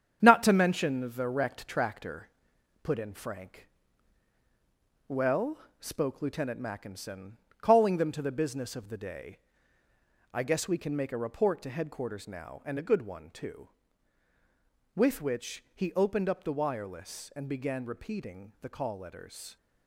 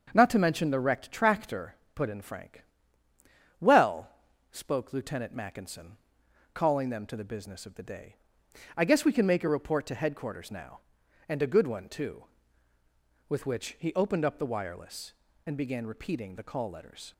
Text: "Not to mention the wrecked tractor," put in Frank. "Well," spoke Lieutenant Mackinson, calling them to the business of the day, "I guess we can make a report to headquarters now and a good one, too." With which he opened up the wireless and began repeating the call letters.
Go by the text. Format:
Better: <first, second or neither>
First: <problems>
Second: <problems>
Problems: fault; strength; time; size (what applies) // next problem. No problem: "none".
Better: second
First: gets quieter; throughout; 6.5 dB // starts louder than the rest; strong; until 1.2 s; 8 dB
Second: starts louder than the rest; until 1.1 s; 7 dB